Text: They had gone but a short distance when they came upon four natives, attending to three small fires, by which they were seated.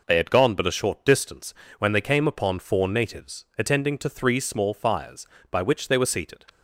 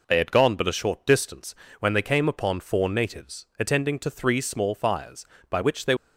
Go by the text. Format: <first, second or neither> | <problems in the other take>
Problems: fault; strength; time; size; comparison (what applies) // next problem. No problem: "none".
first | pauses between "distance" and "when"; slight; at 1.5 s; 0.26 s long; slight in the first // stops before "were seated"; at 5.9 s